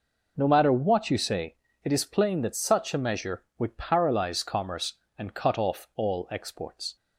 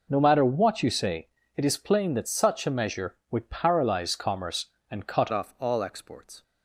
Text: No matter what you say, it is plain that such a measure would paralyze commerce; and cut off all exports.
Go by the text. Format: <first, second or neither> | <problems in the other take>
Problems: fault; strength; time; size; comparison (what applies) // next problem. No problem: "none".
first | changes voice at "off"; from 5.3 s on; 1.1 s long